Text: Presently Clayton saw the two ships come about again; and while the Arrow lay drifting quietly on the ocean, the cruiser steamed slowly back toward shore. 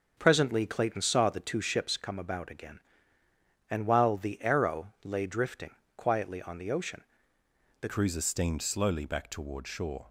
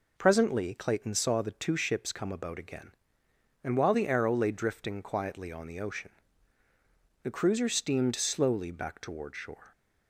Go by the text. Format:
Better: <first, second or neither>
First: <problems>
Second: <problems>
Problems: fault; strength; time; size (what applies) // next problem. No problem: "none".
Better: second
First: starts louder than the rest; until 1.1 s; 6 dB // pauses between "drifting" and "quietly"; slight; at 5.7 s; 0.22 s long // changes voice at "cruiser"; from 7.8 s on; 2.2 s long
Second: none